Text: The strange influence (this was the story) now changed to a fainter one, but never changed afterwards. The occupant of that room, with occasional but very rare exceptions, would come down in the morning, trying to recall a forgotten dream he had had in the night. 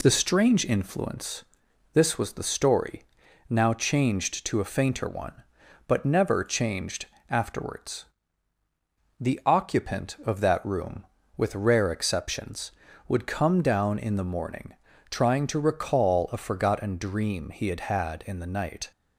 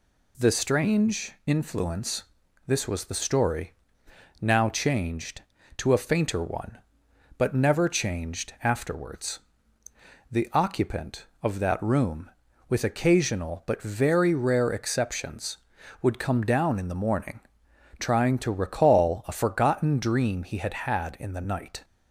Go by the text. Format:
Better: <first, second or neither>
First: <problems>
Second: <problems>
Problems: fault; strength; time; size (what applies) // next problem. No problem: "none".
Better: second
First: pauses between "changed" and "afterwards"; slight; at 7.0 s; 0.26 s long // skips "occasional but very"; at 11.5 s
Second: none